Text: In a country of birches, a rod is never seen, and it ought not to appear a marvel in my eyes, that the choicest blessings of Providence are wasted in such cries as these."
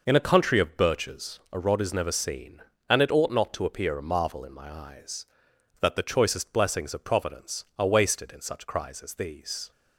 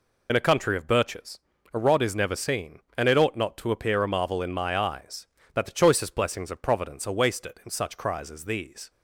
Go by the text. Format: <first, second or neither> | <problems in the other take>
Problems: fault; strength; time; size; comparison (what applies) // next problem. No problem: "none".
first | loses the start of "In"; at 0.2 s; 40 ms